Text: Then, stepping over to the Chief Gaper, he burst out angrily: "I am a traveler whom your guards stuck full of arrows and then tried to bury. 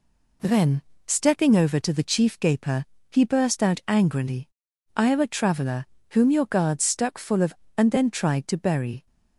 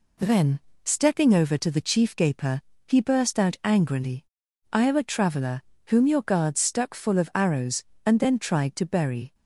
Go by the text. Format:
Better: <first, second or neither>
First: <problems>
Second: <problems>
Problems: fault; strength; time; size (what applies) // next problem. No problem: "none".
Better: second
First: pauses between "traveler" and "whom"; slight; at 5.8 s; 0.26 s long // skips "arrows"; at 7.6 s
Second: pauses between "traveler" and "whom"; slight; at 5.6 s; 0.26 s long